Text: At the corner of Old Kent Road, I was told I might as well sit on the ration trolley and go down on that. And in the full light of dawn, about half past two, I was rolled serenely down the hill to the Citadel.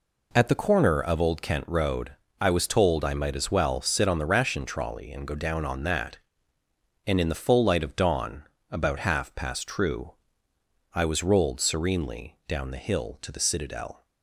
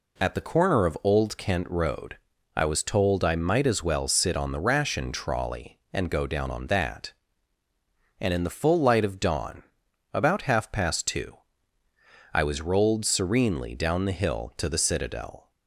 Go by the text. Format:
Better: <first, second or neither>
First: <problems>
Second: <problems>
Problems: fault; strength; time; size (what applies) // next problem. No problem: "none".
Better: second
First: says "true" for "two"; at 9.6 s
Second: none